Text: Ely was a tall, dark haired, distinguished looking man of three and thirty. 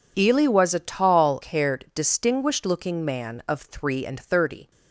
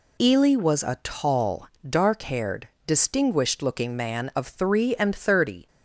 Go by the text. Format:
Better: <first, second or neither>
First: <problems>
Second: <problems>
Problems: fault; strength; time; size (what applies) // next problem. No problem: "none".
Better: second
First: skips "dark"; at 1.4 s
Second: none